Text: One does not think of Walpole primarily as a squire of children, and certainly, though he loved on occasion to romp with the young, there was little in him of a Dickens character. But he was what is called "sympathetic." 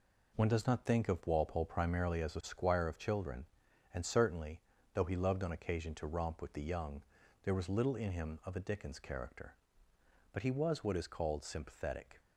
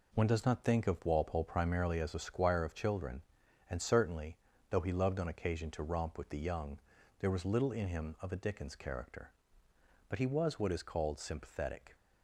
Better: neither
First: none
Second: none

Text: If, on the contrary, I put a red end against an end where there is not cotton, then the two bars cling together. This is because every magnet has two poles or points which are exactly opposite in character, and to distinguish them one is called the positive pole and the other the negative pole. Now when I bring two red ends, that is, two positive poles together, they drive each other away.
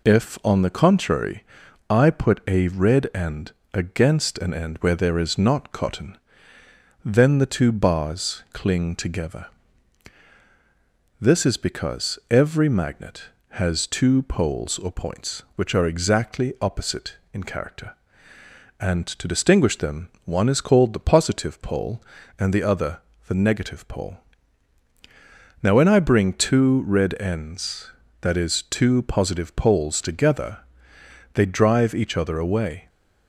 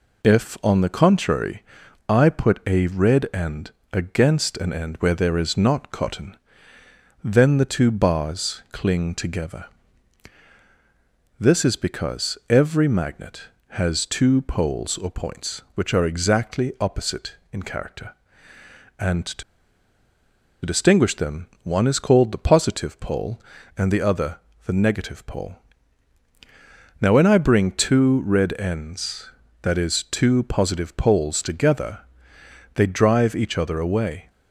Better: first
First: pauses between "end" and "against"; slight; at 3.5 s; 0.22 s long // pauses between "other" and "the"; slight; at 23.0 s; 0.26 s long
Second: pauses between "end" and "against"; slight; at 3.7 s; 0.22 s long // pauses between "to" and "distinguish"; at 19.4 s; 1.2 s long // pauses between "other" and "the"; slight; at 24.3 s; 0.26 s long

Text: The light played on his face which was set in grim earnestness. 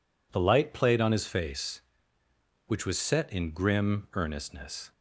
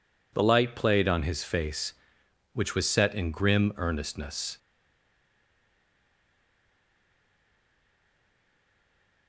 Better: first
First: none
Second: stays silent after the last word; strong; from 4.5 s on; 4.7 s long

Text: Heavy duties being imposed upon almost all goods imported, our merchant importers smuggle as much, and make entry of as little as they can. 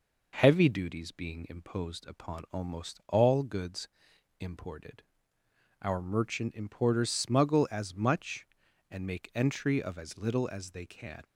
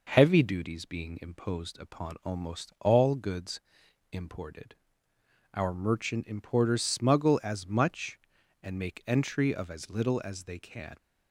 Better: neither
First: pauses between "goods" and "imported"; noticeable; at 3.8 s; 0.54 s long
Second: pauses between "goods" and "imported"; noticeable; at 3.5 s; 0.54 s long

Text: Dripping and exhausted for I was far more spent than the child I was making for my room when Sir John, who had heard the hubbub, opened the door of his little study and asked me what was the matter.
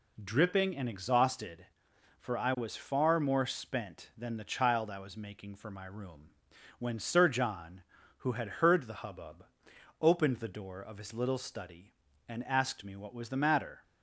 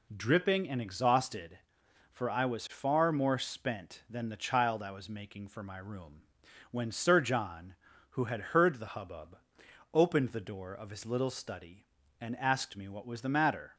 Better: neither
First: pauses between "room" and "when"; noticeable; at 6.3 s; 0.48 s long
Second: pauses between "room" and "when"; noticeable; at 6.2 s; 0.48 s long

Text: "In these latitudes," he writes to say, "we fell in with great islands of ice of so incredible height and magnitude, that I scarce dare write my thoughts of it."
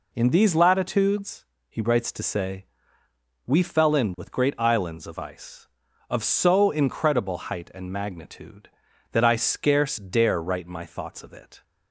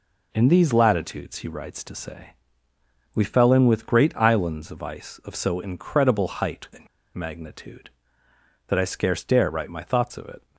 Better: first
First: none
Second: pauses between "and" and "magnitude"; slight; at 6.8 s; 0.27 s long

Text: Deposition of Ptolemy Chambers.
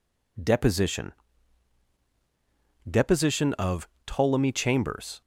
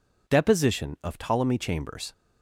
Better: second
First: says "Deposition" twice; at 2.8 s // pauses between "of" and "Ptolemy"; slight; at 3.8 s; 0.18 s long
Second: none

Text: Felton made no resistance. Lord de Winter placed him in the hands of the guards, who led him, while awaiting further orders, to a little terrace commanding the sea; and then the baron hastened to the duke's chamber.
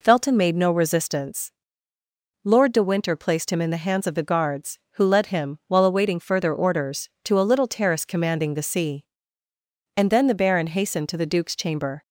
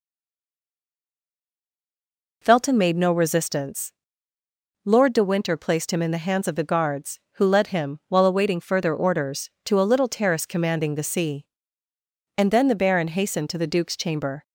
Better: first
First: none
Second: stays silent before the first word; until 2.4 s; 2.4 s long

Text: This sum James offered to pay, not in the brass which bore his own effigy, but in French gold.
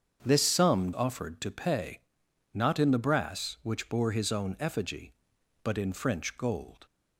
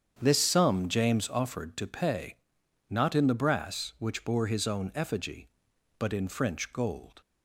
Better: second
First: starts louder than the rest; strong; until 1.2 s; 7.5 dB // skips "James"; at 0.9 s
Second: starts louder than the rest; strong; until 1.2 s; 8 dB

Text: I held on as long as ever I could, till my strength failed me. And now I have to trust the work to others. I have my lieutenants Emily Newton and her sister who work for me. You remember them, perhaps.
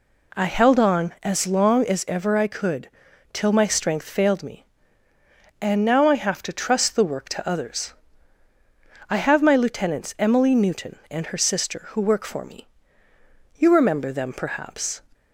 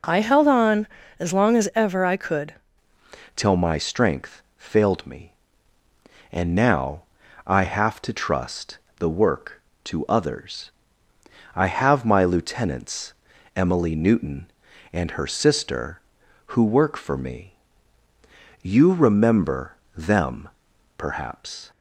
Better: first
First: none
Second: changes voice at "till"; from 3.3 s on; 18.4 s long // pauses between "strength" and "failed"; slight; at 4.4 s; 0.18 s long // pauses between "now" and "I"; at 7.0 s; 0.44 s long // pauses between "trust" and "the"; slight; at 8.7 s; 0.20 s long // pauses between "lieutenants" and "Emily"; at 13.1 s; 0.42 s long // pauses between "remember" and "them"; slight; at 19.7 s; 0.22 s long

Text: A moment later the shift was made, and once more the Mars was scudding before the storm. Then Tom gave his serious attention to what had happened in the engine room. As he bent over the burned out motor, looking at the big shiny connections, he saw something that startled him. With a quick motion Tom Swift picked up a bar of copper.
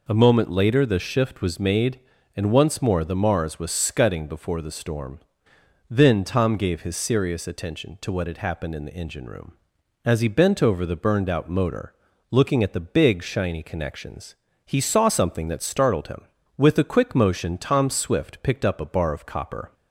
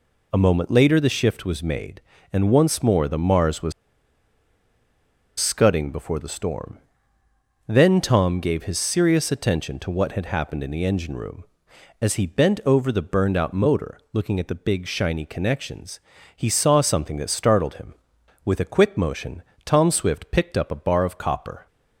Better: first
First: none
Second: pauses between "was" and "scudding"; strong; at 3.7 s; 1.6 s long // pauses between "motion" and "Tom"; slight; at 19.4 s; 0.22 s long

